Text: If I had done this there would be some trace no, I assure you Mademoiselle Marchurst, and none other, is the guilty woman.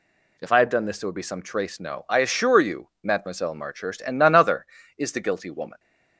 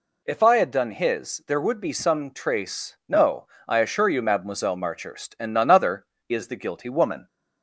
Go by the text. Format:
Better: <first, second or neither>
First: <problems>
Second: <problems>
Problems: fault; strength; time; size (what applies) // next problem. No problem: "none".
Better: first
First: none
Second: says "his" for "this"; at 0.9 s